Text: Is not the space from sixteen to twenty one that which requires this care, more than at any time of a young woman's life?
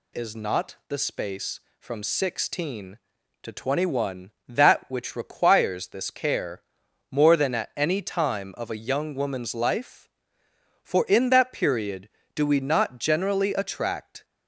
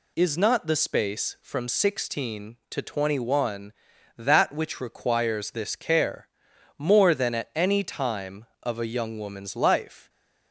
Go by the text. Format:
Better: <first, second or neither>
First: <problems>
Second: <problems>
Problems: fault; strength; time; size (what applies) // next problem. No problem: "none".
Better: second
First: goes on to say "For in that period do we not generally attract"; strong; from 10.8 s on; 3.4 s long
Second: none